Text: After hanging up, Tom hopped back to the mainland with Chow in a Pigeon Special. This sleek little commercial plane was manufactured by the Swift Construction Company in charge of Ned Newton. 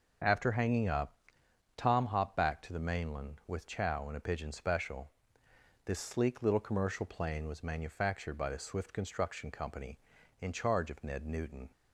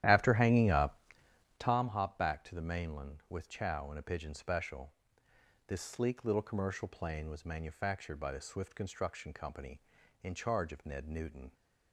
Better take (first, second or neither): first